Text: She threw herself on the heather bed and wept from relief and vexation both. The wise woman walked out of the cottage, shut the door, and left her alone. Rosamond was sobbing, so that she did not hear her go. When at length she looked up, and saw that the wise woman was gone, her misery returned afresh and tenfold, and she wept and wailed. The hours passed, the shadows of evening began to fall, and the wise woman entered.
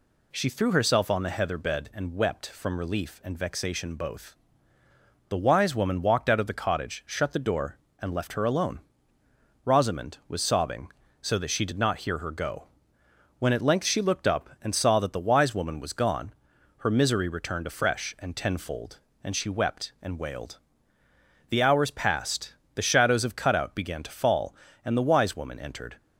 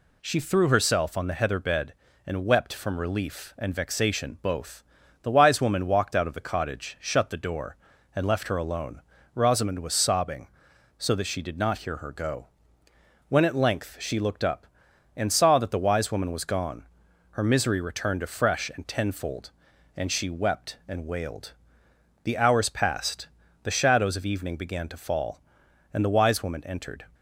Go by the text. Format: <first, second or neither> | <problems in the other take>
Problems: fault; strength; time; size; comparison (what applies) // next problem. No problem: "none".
second | says "cutout" for "evening"; at 23.3 s